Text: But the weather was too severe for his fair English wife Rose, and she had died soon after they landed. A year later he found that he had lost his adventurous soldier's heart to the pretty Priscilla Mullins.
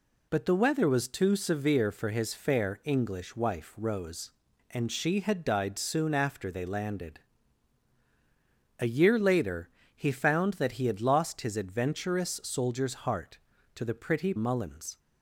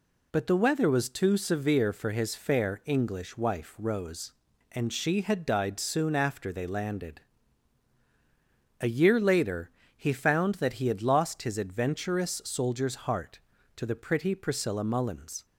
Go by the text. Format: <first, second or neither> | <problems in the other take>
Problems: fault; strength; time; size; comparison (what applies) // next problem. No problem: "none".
second | pauses between "later" and "he"; slight; at 9.6 s; 0.28 s long; slight in the second // skips "Priscilla"; at 14.3 s